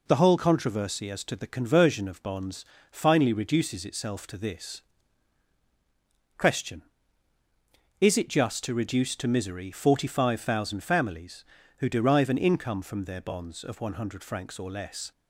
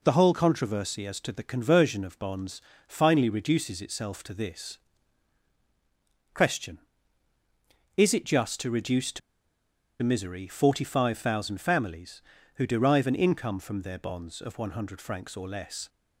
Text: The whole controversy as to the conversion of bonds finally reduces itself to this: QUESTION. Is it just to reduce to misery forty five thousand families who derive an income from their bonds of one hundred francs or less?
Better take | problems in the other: first | pauses between "bonds" and "finally"; slight; at 2.6 s; 0.28 s long; slight in the first // pauses between "to" and "misery"; noticeable; at 9.2 s; 0.82 s long

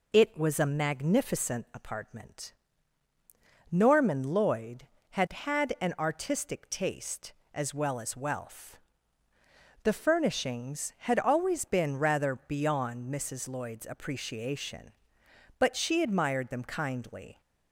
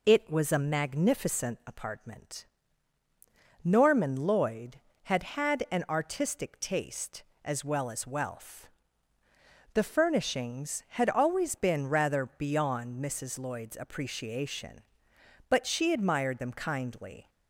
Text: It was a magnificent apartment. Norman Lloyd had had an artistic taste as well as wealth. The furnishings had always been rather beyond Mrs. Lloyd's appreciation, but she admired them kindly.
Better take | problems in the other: neither | none

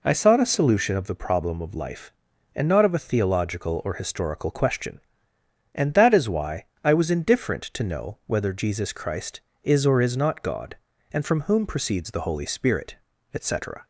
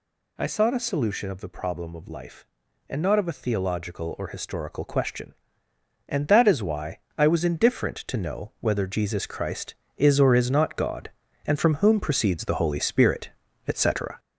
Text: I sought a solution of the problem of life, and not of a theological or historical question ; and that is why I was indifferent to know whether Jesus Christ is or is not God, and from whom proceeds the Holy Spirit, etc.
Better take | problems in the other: first | gets louder; noticeable; throughout; 5 dB // pauses between "why" and "I"; slight; at 6.9 s; 0.22 s long; slight in the first

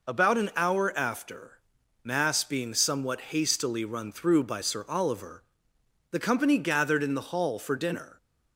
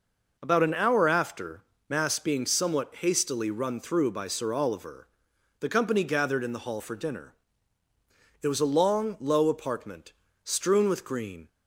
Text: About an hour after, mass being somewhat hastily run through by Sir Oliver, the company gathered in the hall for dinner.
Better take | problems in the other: first | goes on to say "It was a long low apartment strewn with green"; strong; from 8.4 s on; 3.0 s long

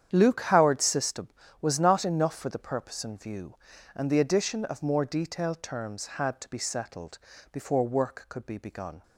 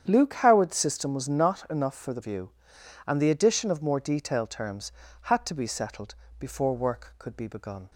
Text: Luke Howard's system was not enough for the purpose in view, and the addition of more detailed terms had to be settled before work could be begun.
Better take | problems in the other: first | starts louder than the rest; strong; until 1.0 s; 8.5 dB; strong in the first // skips "purpose in"; at 2.2 s // pauses between "settled" and "before"; slight; at 6.1 s; 0.24 s long; slight in the first

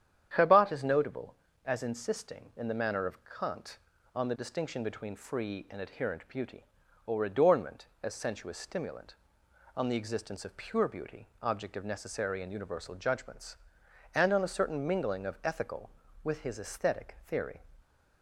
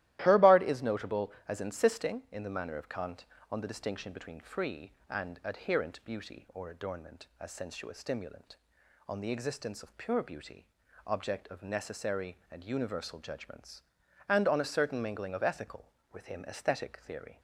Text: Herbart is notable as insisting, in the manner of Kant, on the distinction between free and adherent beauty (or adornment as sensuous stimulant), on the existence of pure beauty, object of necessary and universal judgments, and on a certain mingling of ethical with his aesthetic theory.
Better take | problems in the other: first | starts louder than the rest; strong; until 1.2 s; 15 dB; strong in the first // says "him" for "his"; at 16.2 s

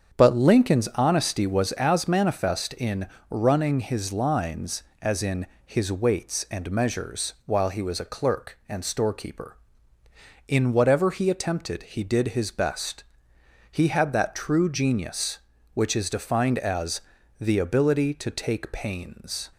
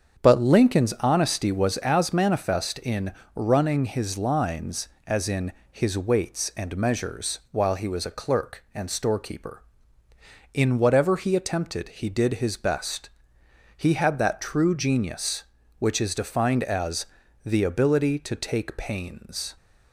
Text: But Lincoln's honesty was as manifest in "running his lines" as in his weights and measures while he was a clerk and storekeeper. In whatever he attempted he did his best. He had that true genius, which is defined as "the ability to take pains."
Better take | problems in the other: neither | starts louder than the rest; the same in both // pauses between "in" and "running"; slight; the same in both // pauses between "in" and "his"; slight; the same in both // pauses between "as" and "the"; the same in both

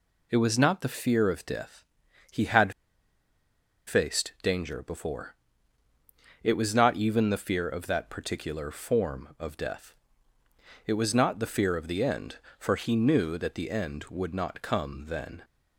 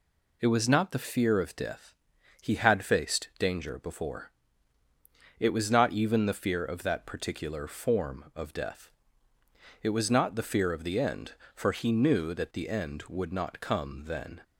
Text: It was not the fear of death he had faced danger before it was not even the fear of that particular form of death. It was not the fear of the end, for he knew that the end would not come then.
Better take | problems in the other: second | pauses between "death" and "he"; noticeable; at 1.8 s; 0.48 s long; noticeable in the second // pauses between "had" and "faced"; at 2.7 s; 1.1 s long // pauses between "before" and "it"; at 5.3 s; 1.0 s long; also in the second

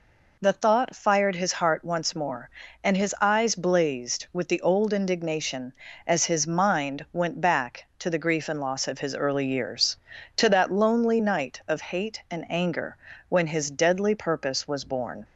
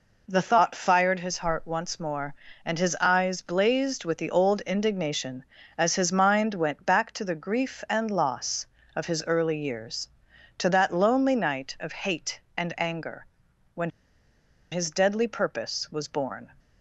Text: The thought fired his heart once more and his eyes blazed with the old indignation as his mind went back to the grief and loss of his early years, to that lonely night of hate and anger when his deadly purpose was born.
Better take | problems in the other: first | pauses between "anger" and "when"; noticeable; at 13.2 s; 0.48 s long; slight in the first // pauses between "when" and "his"; noticeable; at 13.9 s; 0.81 s long

